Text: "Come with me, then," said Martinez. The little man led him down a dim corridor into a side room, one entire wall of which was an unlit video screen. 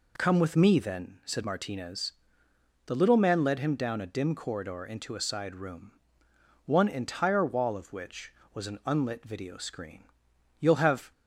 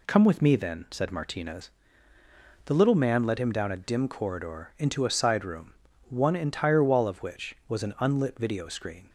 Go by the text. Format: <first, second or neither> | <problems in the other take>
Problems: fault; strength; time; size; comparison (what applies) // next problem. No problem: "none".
second | goes on to say "You'll have"; from 10.5 s on; 0.52 s long